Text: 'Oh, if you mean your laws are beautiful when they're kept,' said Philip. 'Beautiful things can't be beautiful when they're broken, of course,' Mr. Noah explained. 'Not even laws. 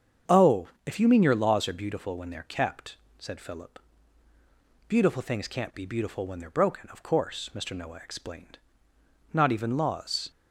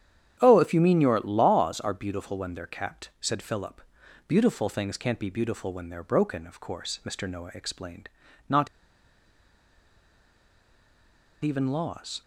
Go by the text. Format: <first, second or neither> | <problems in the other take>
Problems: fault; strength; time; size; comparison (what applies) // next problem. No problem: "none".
first | starts louder than the rest; strong; until 1.4 s; 9 dB; strong in the first // pauses between "Not" and "even"; strong; at 8.6 s; 2.7 s long